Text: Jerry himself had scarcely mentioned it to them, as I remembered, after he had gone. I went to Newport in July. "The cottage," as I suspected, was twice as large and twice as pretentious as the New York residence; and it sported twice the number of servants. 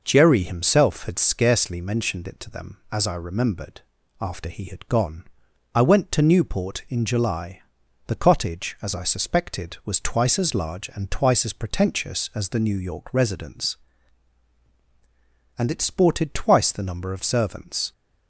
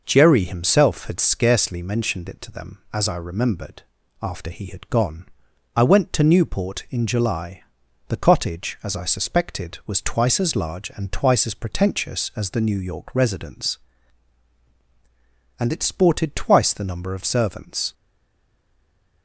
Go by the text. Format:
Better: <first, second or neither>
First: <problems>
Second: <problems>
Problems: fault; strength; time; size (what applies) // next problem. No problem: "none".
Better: first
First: none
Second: stays silent after the last word; noticeable; from 17.9 s on; 1.3 s long